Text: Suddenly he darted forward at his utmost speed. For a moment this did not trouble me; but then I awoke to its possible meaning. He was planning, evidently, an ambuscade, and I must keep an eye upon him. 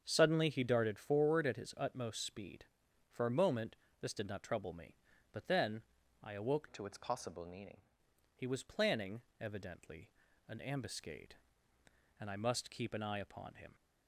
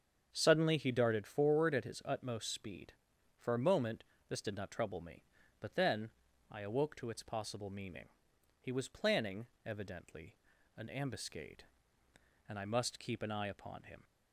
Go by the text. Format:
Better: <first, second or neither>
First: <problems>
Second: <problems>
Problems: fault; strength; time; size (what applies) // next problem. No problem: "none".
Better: second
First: starts louder than the rest; strong; until 1.0 s; 7.5 dB // pauses between "moment" and "this"; slight; at 3.7 s; 0.24 s long // pauses between "then" and "I"; at 5.8 s; 0.42 s long // changes voice from "to" to "meaning"; from 6.7 to 7.8 s; 1.1 s long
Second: starts louder than the rest; strong; until 1.3 s; 7.5 dB // pauses between "moment" and "this"; slight; at 4.0 s; 0.24 s long // pauses between "then" and "I"; at 6.0 s; 0.42 s long